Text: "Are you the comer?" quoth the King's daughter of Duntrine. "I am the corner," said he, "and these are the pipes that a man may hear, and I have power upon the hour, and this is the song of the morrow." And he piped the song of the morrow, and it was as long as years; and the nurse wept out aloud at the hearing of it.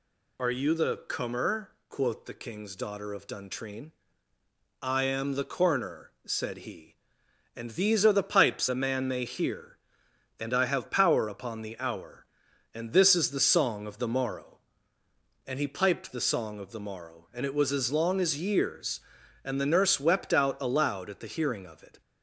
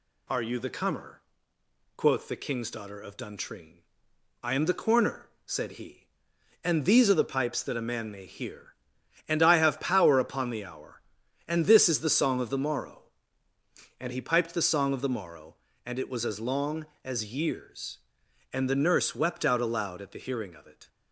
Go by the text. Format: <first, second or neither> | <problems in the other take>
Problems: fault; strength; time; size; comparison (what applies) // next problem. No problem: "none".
second | skips "that"; at 8.6 s